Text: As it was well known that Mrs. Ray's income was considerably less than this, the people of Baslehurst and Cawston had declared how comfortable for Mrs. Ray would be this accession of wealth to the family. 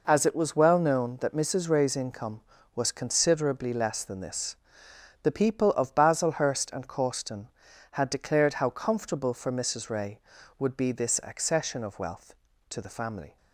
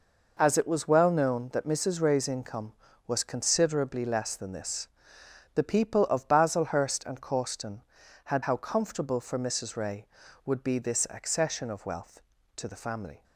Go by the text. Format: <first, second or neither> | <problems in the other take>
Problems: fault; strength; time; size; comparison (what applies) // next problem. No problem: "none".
first | skips "declared"; at 8.4 s